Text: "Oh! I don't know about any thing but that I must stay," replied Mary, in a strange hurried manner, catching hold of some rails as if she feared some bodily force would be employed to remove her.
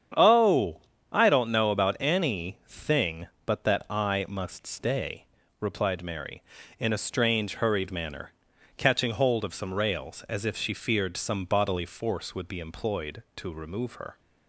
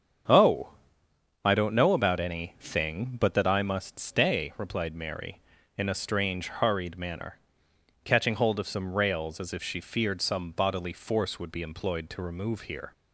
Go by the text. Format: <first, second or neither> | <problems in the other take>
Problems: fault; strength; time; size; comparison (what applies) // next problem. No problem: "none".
first | starts louder than the rest; strong; until 2.0 s; 7.5 dB; strong in the first // says "here" for "her"; at 12.6 s